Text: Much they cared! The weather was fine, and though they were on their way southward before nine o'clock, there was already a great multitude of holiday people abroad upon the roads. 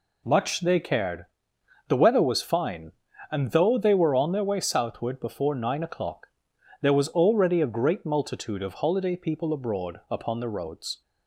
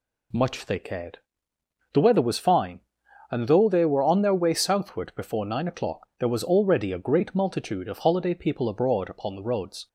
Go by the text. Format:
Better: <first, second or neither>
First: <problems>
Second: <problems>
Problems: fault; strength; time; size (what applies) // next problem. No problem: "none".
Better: neither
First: none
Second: none